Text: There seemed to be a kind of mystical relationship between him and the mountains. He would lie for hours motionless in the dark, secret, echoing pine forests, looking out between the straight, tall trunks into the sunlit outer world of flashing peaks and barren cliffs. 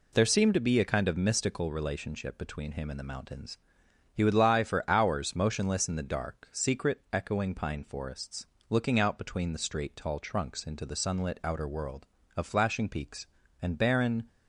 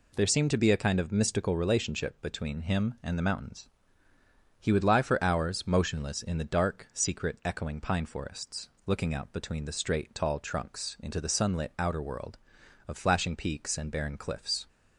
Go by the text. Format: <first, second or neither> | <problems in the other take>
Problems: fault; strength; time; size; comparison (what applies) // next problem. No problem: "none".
second | stops before "cliffs"; at 14.2 s